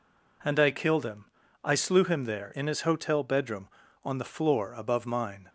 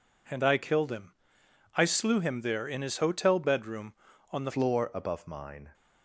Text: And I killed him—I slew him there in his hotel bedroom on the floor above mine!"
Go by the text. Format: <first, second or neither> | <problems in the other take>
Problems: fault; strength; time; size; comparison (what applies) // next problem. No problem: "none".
first | changes voice at "floor"; from 4.4 s on; 1.3 s long